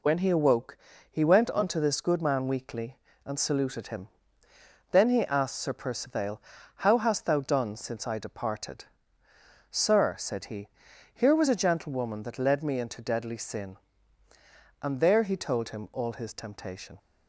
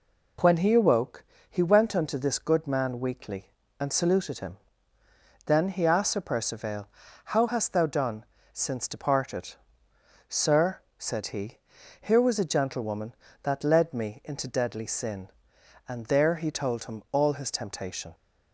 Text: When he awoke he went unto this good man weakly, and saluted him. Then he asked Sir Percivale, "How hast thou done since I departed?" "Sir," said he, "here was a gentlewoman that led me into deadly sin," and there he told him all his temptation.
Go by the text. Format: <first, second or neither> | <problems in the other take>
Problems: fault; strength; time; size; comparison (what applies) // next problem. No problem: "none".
first | pauses between "awoke" and "he"; slight; at 1.2 s; 0.26 s long; slight in the first // pauses between "done" and "since"; slight; at 8.2 s; 0.30 s long // skips "I"; at 8.8 s